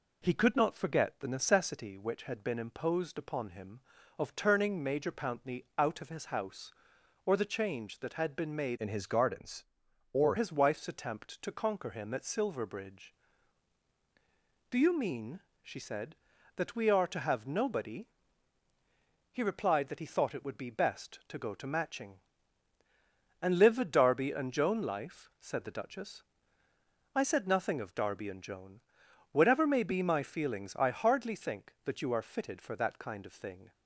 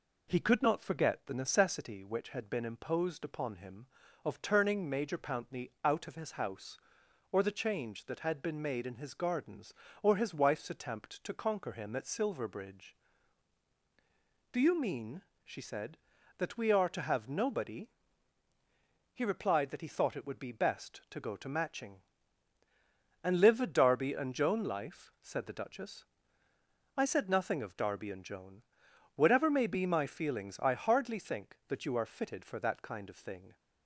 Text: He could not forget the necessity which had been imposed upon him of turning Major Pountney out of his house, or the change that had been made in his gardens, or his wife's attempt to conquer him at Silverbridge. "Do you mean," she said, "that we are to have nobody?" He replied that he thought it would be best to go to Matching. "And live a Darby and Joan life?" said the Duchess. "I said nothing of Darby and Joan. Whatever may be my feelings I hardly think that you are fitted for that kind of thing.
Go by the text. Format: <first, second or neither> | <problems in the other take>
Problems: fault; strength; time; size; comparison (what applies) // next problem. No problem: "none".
second | changes voice from "in" to "or"; from 8.7 to 10.3 s; 1.6 s long